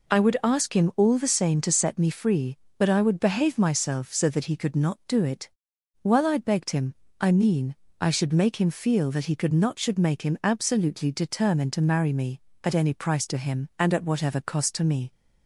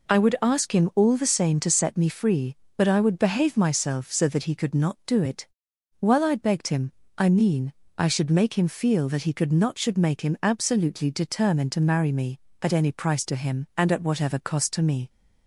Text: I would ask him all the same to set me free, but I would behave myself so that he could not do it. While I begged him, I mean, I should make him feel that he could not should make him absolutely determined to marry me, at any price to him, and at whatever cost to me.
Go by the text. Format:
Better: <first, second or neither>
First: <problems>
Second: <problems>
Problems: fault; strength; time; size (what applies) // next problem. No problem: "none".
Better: neither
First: none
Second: none